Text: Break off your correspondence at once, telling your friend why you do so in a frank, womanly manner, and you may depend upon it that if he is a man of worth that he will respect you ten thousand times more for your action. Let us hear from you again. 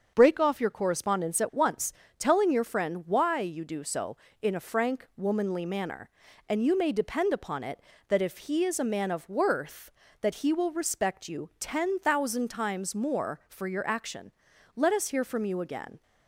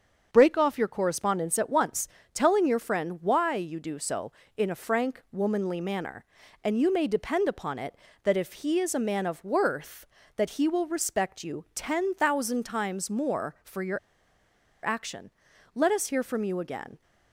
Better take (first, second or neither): first